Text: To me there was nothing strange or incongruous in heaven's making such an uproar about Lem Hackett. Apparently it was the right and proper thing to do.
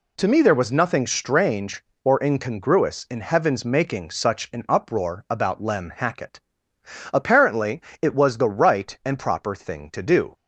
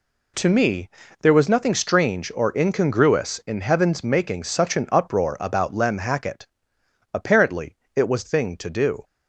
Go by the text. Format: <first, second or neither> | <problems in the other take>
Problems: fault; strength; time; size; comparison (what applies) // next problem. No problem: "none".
first | pauses between "me" and "there"; slight; at 0.8 s; 0.32 s long // pauses between "Apparently" and "it"; slight; at 7.7 s; 0.18 s long; slight in the first // skips "the right and proper"; at 8.2 s